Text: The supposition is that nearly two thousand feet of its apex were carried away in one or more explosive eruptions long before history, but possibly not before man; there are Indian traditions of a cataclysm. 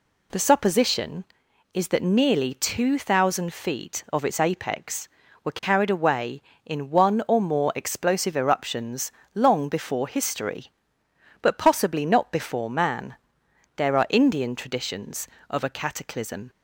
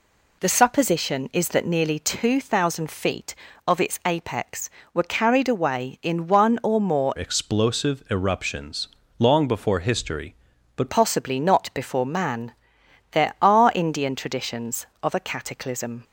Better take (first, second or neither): first